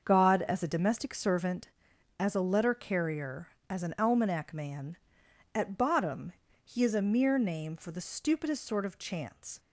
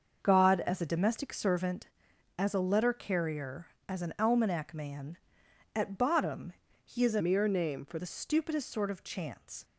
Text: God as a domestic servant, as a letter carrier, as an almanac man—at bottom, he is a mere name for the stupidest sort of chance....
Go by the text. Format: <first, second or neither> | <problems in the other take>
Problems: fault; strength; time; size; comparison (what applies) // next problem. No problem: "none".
first | starts louder than the rest; until 1.2 s; 6.5 dB; also in the first // changes voice from "mere" to "for"; from 7.2 to 7.9 s; 0.7 s long